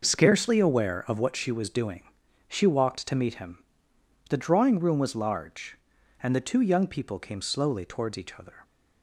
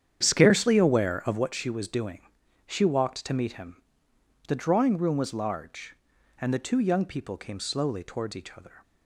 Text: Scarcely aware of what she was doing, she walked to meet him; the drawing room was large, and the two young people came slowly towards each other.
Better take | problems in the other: first | starts louder than the rest; strong; until 1.4 s; 8.5 dB

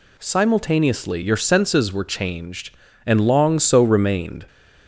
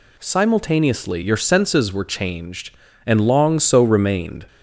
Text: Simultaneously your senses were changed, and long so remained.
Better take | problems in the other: neither | none

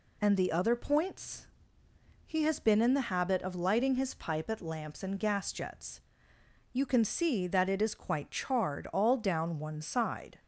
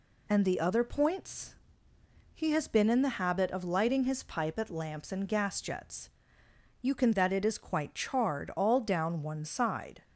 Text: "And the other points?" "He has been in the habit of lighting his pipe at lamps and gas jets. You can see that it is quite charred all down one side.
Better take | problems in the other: first | skips "see"; at 7.1 s

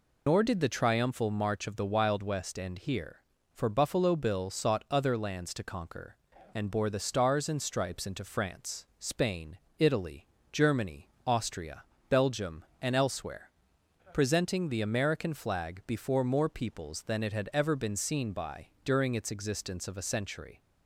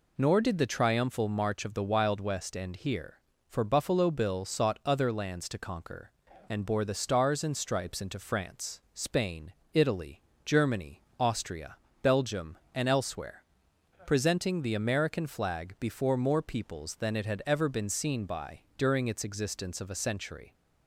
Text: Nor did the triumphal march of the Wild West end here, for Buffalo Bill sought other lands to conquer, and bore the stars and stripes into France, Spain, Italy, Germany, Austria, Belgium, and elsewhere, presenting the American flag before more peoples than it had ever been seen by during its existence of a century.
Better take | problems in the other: second | loses the start of "Nor"; at 0.2 s; 60 ms

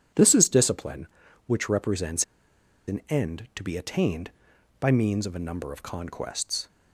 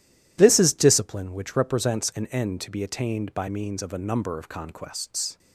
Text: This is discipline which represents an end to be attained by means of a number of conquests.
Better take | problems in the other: second | pauses between "represents" and "an"; noticeable; at 2.2 s; 0.65 s long

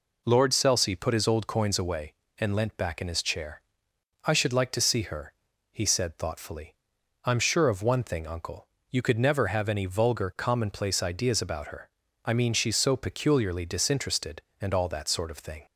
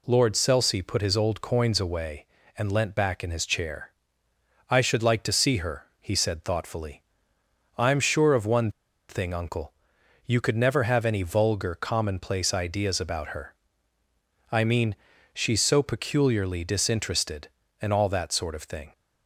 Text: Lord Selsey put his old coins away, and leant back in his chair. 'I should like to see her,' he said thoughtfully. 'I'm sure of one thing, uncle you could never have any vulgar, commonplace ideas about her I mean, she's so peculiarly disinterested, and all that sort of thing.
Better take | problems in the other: first | pauses between "one" and "thing"; at 8.7 s; 0.38 s long // pauses between "uncle" and "you"; noticeable; at 9.7 s; 0.52 s long; slight in the first // pauses between "her" and "I"; noticeable; at 13.5 s; 0.98 s long; slight in the first

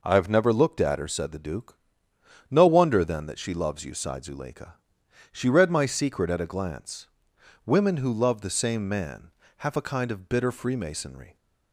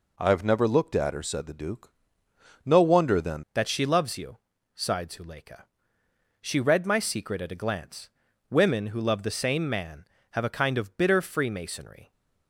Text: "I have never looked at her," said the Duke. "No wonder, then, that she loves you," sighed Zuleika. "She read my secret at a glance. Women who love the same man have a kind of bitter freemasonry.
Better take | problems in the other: first | changes voice at "that"; from 3.5 s on; 8.6 s long

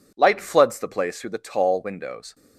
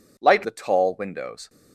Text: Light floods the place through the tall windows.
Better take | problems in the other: first | skips "floods the place through"; at 0.4 s

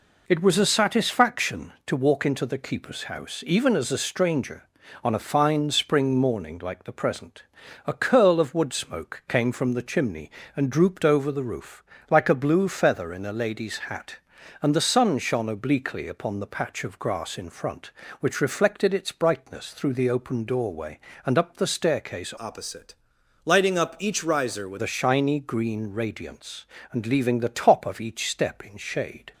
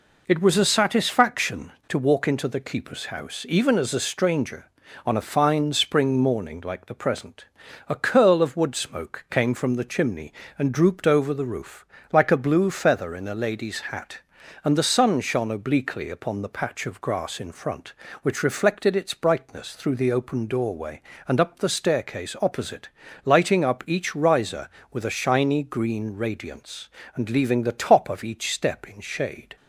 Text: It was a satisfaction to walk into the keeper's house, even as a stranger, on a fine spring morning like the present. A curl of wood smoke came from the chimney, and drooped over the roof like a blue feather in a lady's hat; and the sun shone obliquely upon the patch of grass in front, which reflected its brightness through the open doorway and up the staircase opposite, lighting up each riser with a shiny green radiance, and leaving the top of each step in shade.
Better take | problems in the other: second | pauses between "roof" and "like"; slight; at 11.8 s; 0.26 s long; slight in the second // changes voice from "opposite" to "with"; from 22.3 to 24.8 s; 2.5 s long

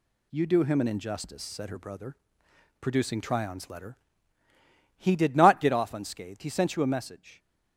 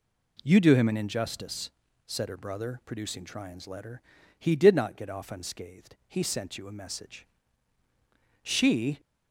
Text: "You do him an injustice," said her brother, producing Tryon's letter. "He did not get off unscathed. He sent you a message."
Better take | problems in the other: first | goes on to say "She"; from 8.4 s on; 0.56 s long

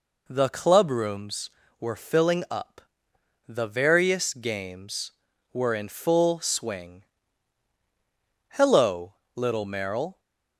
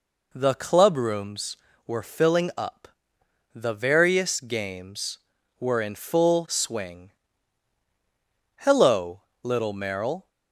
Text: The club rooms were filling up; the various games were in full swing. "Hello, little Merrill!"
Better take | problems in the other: neither | none

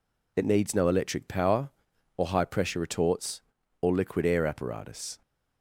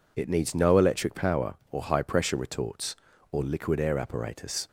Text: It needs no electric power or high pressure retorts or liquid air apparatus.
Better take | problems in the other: neither | none

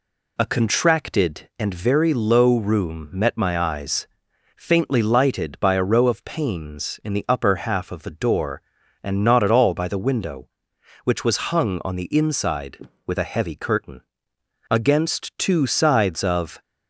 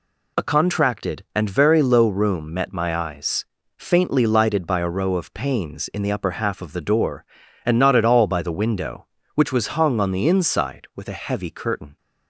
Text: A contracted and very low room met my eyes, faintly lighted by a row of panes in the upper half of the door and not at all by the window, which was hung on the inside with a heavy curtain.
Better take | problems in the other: second | goes on to say "Against two sides of"; strong; from 14.6 s on; 1.9 s long

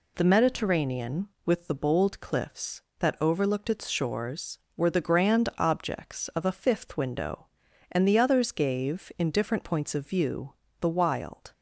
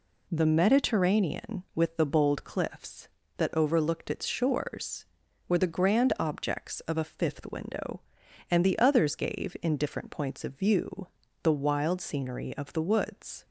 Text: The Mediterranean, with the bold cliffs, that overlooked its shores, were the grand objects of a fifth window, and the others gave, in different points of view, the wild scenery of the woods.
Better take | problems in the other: second | stops before "scenery of the woods"; at 11.5 s

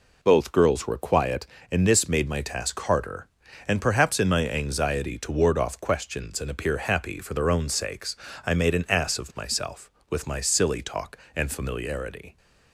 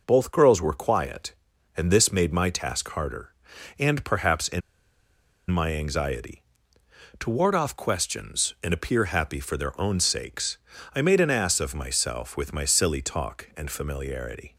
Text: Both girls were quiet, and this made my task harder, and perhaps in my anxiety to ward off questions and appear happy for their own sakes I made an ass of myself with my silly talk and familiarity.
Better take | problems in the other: first | pauses between "in" and "my"; noticeable; at 4.6 s; 0.90 s long // pauses between "sakes" and "I"; at 10.5 s; 0.38 s long; slight in the first

